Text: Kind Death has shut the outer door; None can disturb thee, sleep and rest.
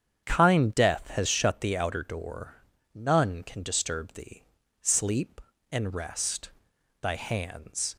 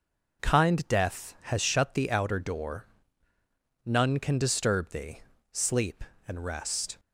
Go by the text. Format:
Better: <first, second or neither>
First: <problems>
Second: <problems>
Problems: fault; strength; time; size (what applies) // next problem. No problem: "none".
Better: second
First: starts louder than the rest; strong; until 1.3 s; 8 dB // goes on to say "Thy hands"; noticeable; from 7.0 s on; 0.94 s long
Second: none